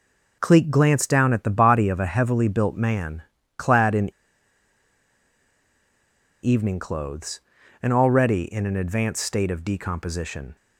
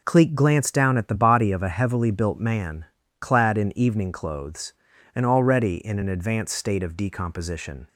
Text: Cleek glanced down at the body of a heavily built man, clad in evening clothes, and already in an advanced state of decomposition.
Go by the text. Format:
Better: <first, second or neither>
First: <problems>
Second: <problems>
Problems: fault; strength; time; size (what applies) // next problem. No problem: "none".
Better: second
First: pauses between "in" and "evening"; strong; at 4.1 s; 2.3 s long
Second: none